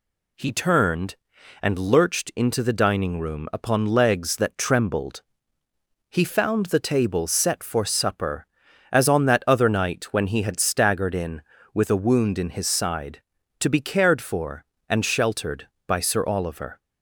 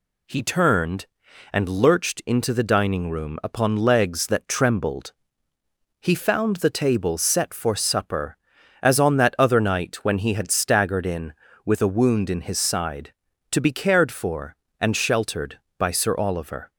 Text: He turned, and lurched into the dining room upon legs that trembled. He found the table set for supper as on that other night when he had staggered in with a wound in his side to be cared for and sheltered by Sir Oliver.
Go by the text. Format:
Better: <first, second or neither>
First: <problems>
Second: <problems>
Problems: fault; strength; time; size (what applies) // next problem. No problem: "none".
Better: neither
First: none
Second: none